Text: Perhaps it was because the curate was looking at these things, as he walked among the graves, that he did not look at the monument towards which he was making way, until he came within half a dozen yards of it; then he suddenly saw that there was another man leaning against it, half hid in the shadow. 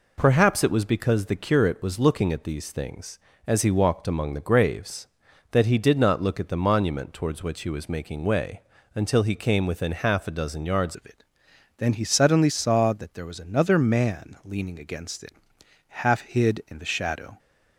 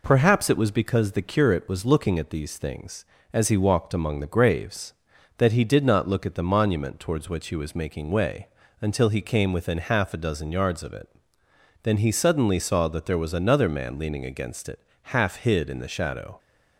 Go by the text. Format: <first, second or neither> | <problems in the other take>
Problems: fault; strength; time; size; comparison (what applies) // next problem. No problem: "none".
second | changes voice at "of"; from 10.9 s on; 6.4 s long